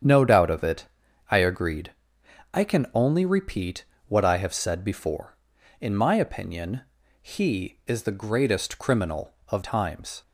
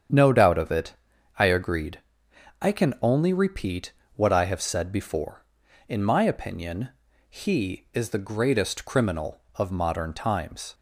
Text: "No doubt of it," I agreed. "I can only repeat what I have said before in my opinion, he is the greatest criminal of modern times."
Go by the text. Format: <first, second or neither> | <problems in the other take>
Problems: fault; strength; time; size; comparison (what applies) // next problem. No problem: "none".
second | starts louder than the rest; strong; until 1.4 s; 8.5 dB; strong in the second // pauses between "repeat" and "what"; slight; at 3.8 s; 0.24 s long; slight in the second // skips "modern"; at 9.6 s